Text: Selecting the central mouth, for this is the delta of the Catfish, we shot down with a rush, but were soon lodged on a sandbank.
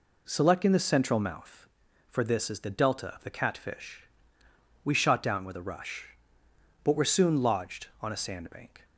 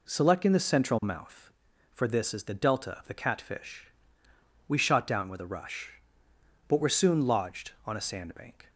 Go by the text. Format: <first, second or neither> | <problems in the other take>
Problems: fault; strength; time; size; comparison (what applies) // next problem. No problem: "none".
neither | none